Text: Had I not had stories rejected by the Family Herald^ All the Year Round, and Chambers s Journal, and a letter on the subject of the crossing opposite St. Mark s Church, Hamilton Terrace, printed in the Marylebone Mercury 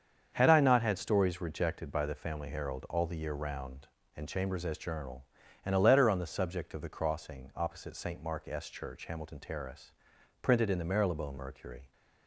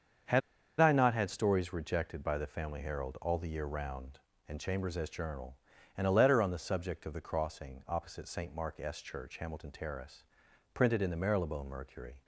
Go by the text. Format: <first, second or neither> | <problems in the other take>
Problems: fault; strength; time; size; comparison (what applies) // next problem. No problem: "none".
first | starts louder than the rest; until 1.6 s; 7 dB; strong in the first // pauses between "Had" and "I"; at 0.4 s; 0.40 s long